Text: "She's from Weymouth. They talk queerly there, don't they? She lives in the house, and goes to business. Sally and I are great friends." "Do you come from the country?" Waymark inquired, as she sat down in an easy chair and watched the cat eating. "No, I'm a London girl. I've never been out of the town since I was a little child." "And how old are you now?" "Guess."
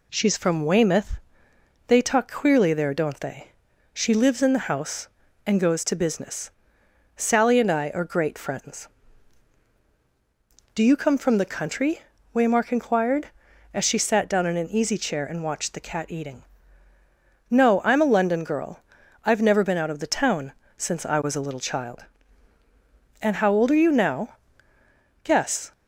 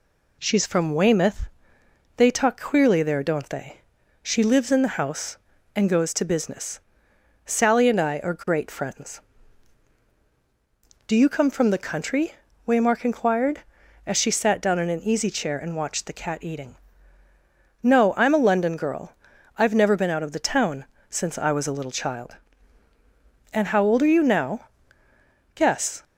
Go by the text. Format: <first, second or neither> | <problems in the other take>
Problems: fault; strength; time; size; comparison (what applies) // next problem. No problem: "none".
neither | pauses between "town" and "since"; slight; the same in both